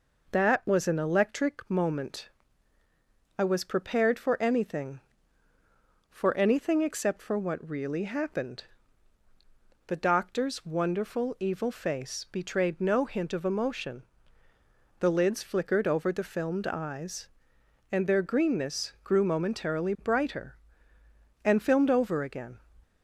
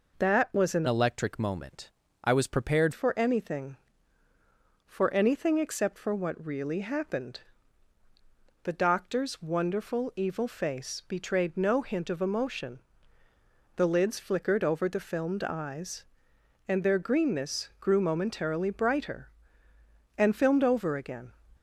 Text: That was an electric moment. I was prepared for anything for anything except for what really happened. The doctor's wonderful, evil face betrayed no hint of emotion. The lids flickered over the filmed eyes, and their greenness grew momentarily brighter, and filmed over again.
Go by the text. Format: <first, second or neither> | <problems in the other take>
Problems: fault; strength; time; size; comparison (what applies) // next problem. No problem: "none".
first | changes voice from "electric" to "prepared"; from 0.8 to 2.9 s; 2.1 s long